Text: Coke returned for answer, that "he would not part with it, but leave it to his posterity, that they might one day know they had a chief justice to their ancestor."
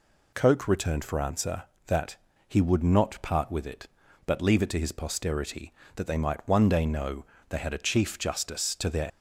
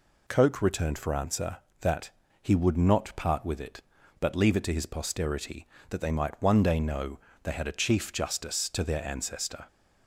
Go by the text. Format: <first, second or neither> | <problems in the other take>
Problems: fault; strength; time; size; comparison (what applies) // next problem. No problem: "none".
second | pauses between "that" and "he"; slight; at 2.1 s; 0.32 s long; slight in the second // pauses between "know" and "they"; slight; at 7.2 s; 0.24 s long; slight in the second // stops before "ancestor"; at 9.0 s